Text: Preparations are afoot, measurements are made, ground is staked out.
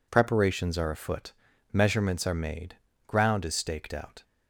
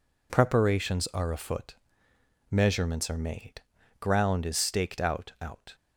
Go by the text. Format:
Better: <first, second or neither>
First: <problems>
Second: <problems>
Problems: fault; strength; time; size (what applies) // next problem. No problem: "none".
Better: first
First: none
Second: says "out" twice; at 5.4 s